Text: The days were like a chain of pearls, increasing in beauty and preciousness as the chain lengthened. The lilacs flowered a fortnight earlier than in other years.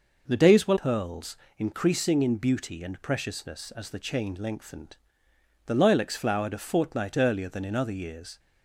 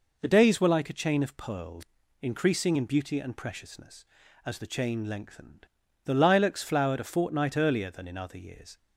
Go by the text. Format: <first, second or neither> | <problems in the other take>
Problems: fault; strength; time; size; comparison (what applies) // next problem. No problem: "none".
second | skips "like a chain of"; at 0.7 s